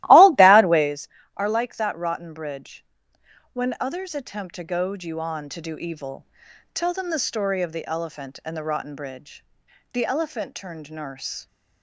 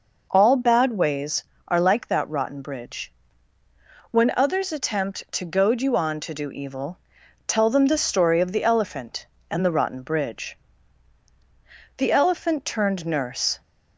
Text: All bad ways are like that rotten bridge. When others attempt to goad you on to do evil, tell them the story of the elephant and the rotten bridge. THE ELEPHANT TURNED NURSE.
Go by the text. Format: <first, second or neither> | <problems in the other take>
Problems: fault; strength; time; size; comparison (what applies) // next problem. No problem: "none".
second | starts louder than the rest; strong; until 1.0 s; 15.5 dB